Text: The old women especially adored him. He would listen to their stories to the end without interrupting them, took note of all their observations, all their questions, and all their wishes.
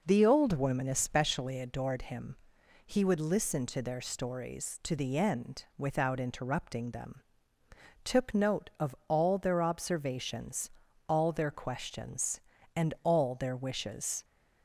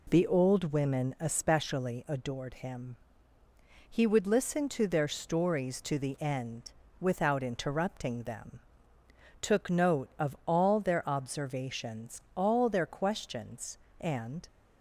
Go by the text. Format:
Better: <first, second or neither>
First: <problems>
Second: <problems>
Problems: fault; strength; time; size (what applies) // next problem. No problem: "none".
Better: first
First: none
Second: pauses between "end" and "without"; slight; at 6.7 s; 0.26 s long // stops before "all their wishes"; at 14.4 s